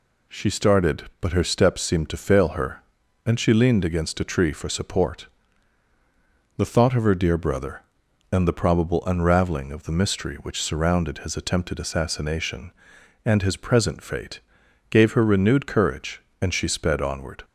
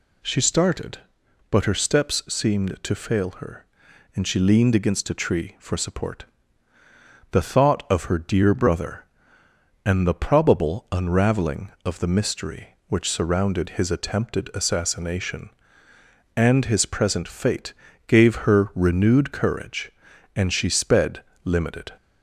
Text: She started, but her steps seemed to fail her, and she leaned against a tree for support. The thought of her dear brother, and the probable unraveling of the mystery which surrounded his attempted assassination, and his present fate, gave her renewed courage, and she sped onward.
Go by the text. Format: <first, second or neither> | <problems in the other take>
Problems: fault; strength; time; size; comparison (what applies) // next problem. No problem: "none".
first | says "limited" for "onward"; at 21.4 s